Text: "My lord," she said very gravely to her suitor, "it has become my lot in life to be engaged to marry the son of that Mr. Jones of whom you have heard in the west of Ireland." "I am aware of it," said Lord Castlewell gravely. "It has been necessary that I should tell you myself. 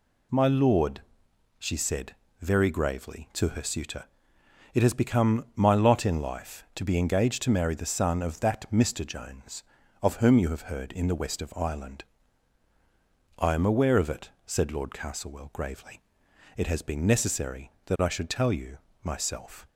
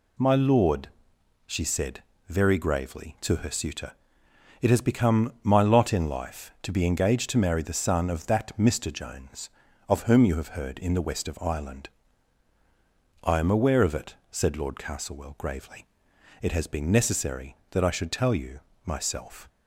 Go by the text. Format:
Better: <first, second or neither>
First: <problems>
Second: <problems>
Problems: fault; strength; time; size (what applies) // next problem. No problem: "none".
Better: neither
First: pauses between "said" and "very"; slight; at 2.1 s; 0.24 s long // pauses between "you" and "myself"; slight; at 18.7 s; 0.26 s long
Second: pauses between "said" and "very"; slight; at 2.0 s; 0.24 s long // pauses between "you" and "myself"; slight; at 18.5 s; 0.26 s long